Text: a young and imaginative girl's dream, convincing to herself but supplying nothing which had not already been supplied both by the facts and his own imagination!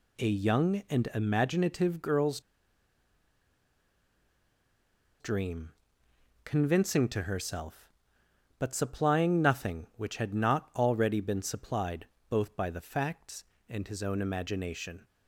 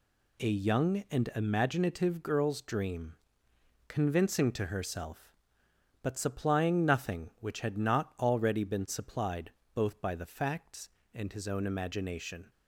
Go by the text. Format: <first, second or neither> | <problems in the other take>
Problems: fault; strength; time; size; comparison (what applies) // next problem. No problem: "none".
second | pauses between "girl's" and "dream"; strong; at 2.3 s; 2.8 s long // pauses between "supplied" and "both"; slight; at 12.0 s; 0.24 s long; slight in the second